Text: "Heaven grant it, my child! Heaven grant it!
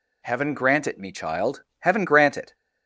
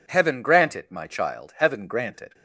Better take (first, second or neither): second